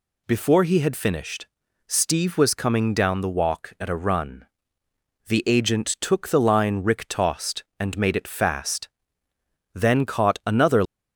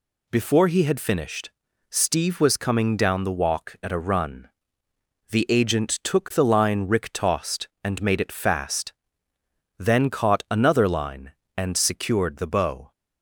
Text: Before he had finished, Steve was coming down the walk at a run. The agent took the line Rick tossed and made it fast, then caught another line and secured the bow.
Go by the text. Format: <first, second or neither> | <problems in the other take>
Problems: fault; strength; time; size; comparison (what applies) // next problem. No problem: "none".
second | stops before "line and secured the bow"; at 10.8 s